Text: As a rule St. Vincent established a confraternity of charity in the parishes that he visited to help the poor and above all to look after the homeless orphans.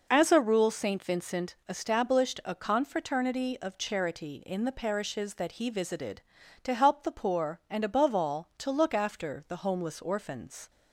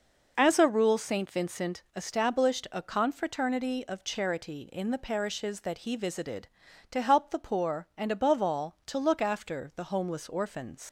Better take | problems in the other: first | leaves "orphans" unfinished; at 10.8 s; 80 ms

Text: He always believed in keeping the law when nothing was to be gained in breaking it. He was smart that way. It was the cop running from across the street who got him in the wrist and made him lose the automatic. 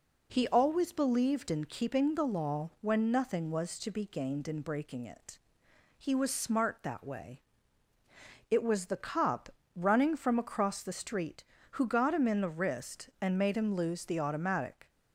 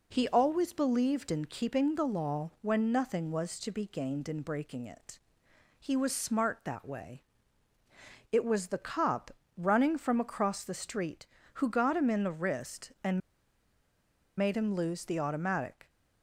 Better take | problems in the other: first | pauses between "cop" and "running"; slight; at 9.3 s; 0.24 s long; slight in the first // pauses between "and" and "made"; at 13.2 s; 1.1 s long

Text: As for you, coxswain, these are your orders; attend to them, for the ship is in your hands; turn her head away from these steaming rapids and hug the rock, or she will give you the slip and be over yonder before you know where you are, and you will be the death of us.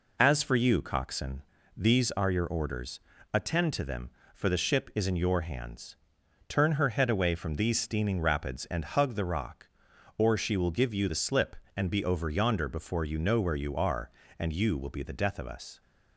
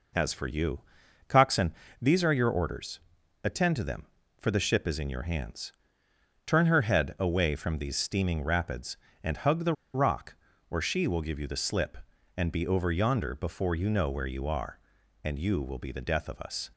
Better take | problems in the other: first | pauses between "the" and "rock"; slight; at 9.7 s; 0.21 s long

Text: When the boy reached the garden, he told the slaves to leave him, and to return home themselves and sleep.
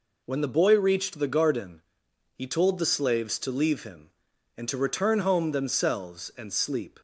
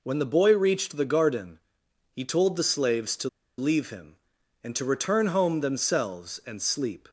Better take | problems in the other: first | pauses between "to" and "leave"; slight; at 3.2 s; 0.29 s long

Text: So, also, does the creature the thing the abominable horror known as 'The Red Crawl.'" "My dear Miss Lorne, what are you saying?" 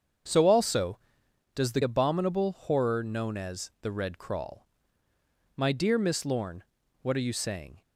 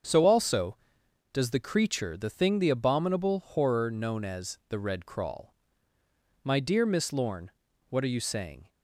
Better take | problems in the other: second | starts louder than the rest; strong; until 1.8 s; 7.5 dB; also in the second // skips "creature the thing the"; at 1.8 s

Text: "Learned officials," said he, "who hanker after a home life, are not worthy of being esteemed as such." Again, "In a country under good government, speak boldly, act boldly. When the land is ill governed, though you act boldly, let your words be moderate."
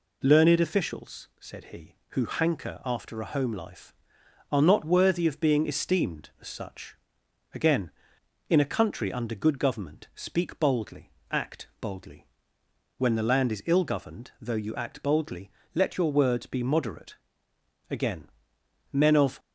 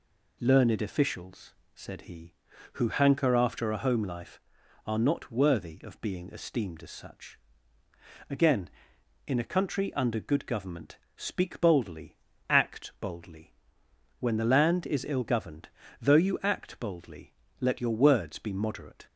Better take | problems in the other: second | goes on to say "Again Men of"; from 17.9 s on; 1.4 s long

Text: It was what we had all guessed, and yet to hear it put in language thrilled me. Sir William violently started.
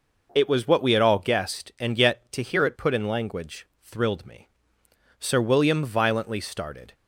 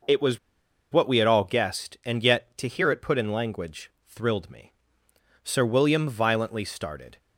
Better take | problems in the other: first | pauses between "was" and "what"; noticeable; at 0.3 s; 0.53 s long // pauses between "language" and "thrilled"; slight; at 3.8 s; 0.18 s long; slight in the first

